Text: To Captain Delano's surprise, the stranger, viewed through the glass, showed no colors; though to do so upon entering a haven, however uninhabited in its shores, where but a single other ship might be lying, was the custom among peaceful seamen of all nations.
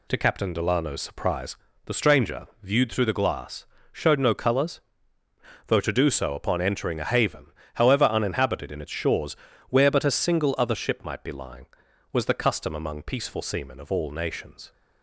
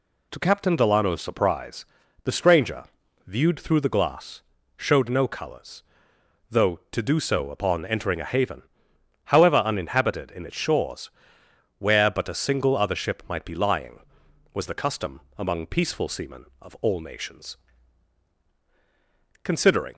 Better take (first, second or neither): first